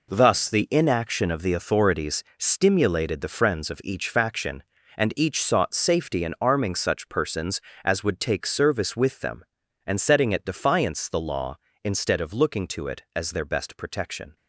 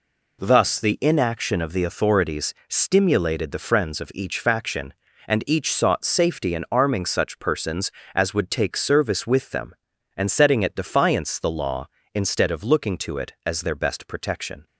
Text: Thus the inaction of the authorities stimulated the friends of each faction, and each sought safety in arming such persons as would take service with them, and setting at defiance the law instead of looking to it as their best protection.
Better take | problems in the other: second | gets quieter; strong; throughout; 10 dB // pauses between "authorities" and "stimulated"; slight; at 2.2 s; 0.16 s long; slight in the second

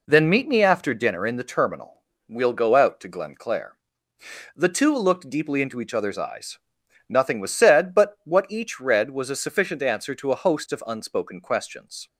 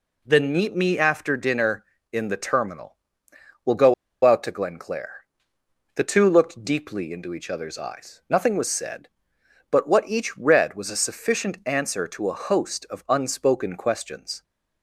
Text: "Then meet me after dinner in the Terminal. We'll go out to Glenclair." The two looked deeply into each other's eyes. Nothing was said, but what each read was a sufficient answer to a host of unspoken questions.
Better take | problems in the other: first | pauses between "go" and "out"; slight; at 3.9 s; 0.30 s long

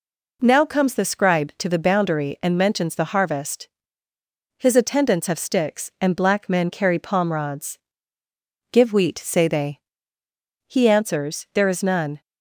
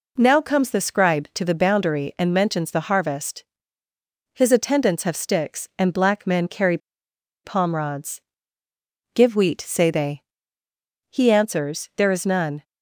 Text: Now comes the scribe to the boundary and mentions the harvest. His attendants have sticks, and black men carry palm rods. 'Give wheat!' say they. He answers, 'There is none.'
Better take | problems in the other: first | pauses between "carry" and "palm"; noticeable; at 6.7 s; 0.66 s long

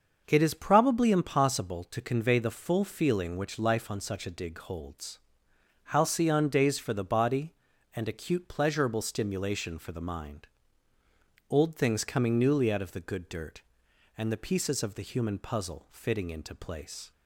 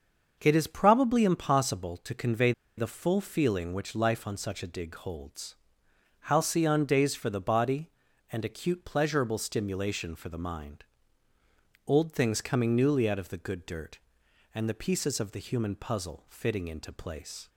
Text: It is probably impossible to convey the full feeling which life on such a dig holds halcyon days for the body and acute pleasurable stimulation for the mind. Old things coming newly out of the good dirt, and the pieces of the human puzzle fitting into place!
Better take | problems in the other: first | starts louder than the rest; until 1.4 s; 6.5 dB; also in the first // pauses between "convey" and "the"; slight; at 2.5 s; 0.26 s long // pauses between "holds" and "halcyon"; noticeable; at 5.5 s; 0.70 s long; noticeable in the first

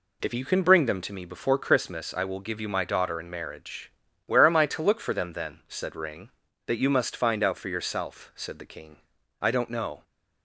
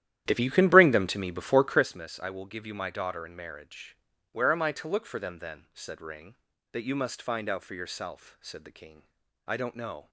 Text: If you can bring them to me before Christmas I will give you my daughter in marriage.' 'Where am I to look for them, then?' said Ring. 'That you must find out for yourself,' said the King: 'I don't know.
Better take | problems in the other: first | starts louder than the rest; strong; until 1.9 s; 11.5 dB

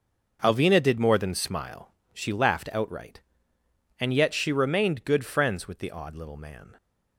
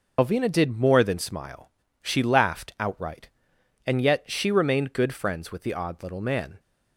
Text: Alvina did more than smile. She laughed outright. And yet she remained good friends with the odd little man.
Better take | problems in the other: first | loses the start of "Alvina"; at 0.1 s; 55 ms

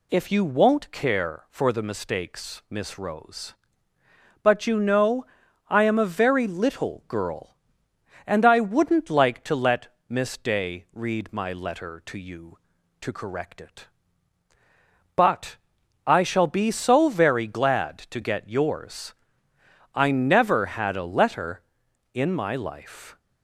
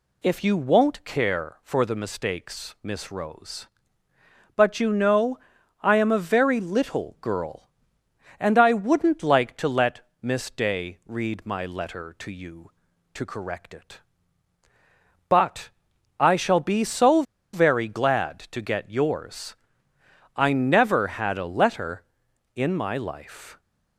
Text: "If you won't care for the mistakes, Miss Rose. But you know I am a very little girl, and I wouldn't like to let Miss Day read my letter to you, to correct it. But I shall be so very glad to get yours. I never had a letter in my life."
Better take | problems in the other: first | pauses between "know" and "I"; at 5.3 s; 0.44 s long; also in the first // pauses between "But" and "I"; noticeable; at 15.7 s; 0.50 s long; noticeable in the first // pauses between "so" and "very"; slight; at 17.2 s; 0.30 s long

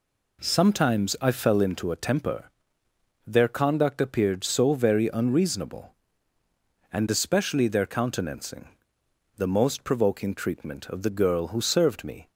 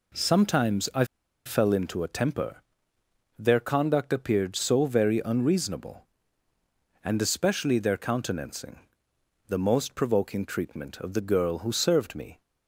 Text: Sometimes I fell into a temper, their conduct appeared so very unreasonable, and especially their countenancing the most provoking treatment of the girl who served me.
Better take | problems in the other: first | pauses between "I" and "fell"; at 1.0 s; 0.40 s long // pauses between "countenancing" and "the"; noticeable; at 8.7 s; 0.70 s long; noticeable in the first

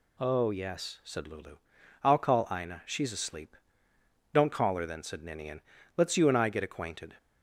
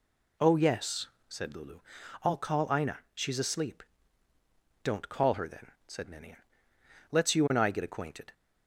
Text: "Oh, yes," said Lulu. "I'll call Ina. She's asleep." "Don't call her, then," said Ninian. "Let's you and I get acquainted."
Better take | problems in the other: neither | none

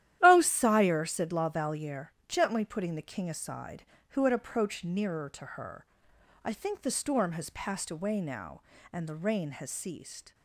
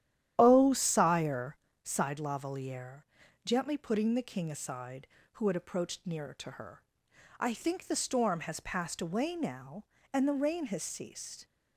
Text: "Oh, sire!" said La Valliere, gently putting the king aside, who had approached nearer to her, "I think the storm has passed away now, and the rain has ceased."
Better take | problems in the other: first | starts louder than the rest; strong; until 1.3 s; 11 dB; strong in the first // says "sighed" for "said"; at 1.8 s

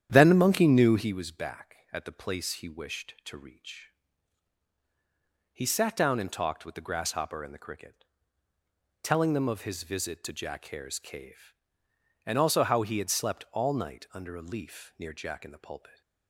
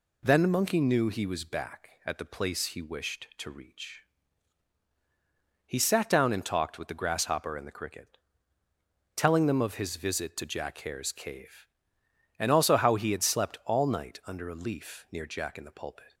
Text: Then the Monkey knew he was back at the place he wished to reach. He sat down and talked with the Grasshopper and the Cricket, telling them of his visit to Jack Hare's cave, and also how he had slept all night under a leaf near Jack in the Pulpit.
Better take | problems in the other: second | starts louder than the rest; strong; until 1.1 s; 9.5 dB

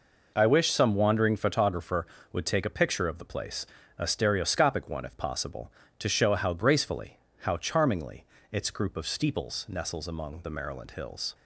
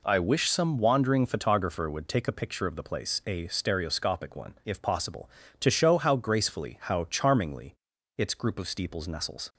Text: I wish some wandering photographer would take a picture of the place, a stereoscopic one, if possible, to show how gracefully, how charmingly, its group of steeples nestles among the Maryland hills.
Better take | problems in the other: first | stops before "among the Maryland hills"; at 9.5 s

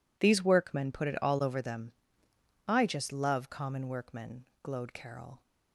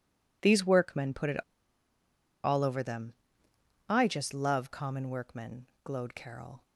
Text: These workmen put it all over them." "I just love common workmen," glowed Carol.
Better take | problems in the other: first | pauses between "it" and "all"; at 1.4 s; 1.0 s long

